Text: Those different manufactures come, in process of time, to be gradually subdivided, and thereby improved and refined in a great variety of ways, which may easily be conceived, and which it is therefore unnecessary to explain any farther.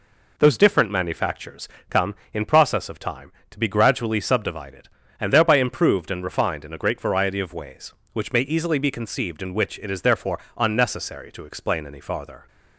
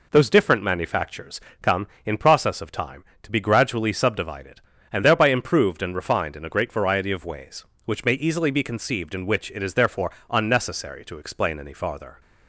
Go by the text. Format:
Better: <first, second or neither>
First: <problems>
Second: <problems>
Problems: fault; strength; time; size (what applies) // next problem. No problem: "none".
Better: neither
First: pauses between "manufactures" and "come"; slight; at 1.6 s; 0.22 s long // pauses between "therefore" and "unnecessary"; slight; at 10.3 s; 0.17 s long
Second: pauses between "manufactures" and "come"; slight; at 1.3 s; 0.22 s long // pauses between "therefore" and "unnecessary"; slight; at 10.1 s; 0.18 s long